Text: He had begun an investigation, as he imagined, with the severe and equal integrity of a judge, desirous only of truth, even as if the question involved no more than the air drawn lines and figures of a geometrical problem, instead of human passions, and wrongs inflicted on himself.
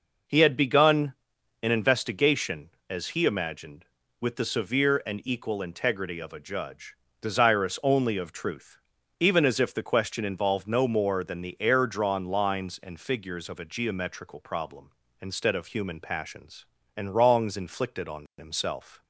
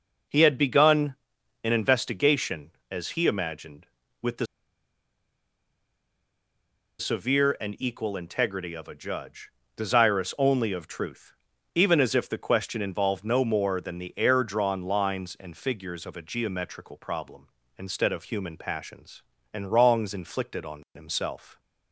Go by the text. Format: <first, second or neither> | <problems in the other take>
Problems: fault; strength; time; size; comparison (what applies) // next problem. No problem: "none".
first | pauses between "begun" and "an"; noticeable; at 1.1 s; 0.50 s long; noticeable in the first // pauses between "the" and "severe"; strong; at 4.4 s; 2.5 s long